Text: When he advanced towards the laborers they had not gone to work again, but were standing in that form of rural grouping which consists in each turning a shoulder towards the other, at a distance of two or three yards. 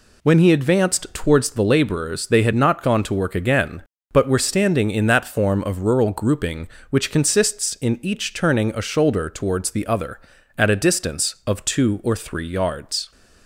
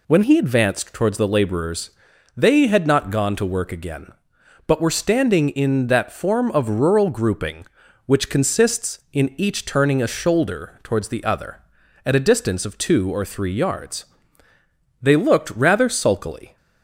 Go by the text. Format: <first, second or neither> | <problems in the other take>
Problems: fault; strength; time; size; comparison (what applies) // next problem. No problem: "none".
first | pauses between "laborers" and "they"; noticeable; at 1.8 s; 0.46 s long // goes on to say "They looked rather sulkily"; from 15.0 s on; 1.5 s long